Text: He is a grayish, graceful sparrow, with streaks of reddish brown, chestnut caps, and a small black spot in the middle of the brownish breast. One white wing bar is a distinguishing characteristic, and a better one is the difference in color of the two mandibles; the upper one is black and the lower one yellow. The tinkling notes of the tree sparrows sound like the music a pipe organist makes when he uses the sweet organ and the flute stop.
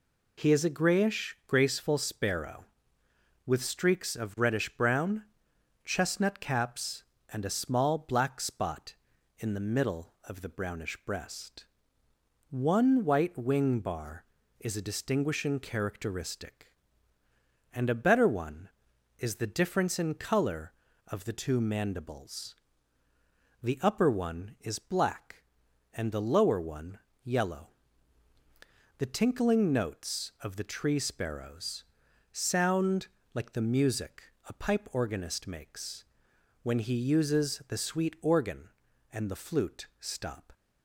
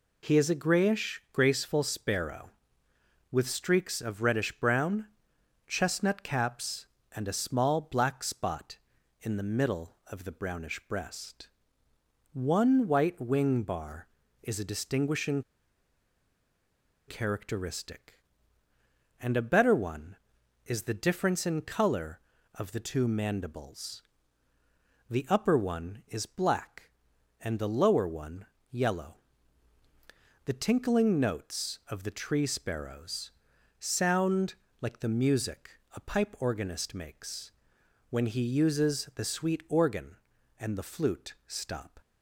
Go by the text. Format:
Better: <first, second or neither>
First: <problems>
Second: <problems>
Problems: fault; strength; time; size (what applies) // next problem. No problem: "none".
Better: first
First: pauses between "one" and "yellow"; slight; at 26.9 s; 0.26 s long // pauses between "sparrows" and "sound"; noticeable; at 31.8 s; 0.46 s long // pauses between "sound" and "like"; slight; at 33.0 s; 0.26 s long // pauses between "music" and "a"; slight; at 34.2 s; 0.22 s long // pauses between "makes" and "when"; noticeable; at 36.0 s; 0.56 s long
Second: pauses between "distinguishing" and "characteristic"; strong; at 15.4 s; 1.6 s long // pauses between "one" and "yellow"; slight; at 28.4 s; 0.26 s long // pauses between "sparrows" and "sound"; noticeable; at 33.3 s; 0.46 s long // pauses between "sound" and "like"; slight; at 34.5 s; 0.26 s long // pauses between "music" and "a"; slight; at 35.7 s; 0.22 s long // pauses between "makes" and "when"; noticeable; at 37.5 s; 0.56 s long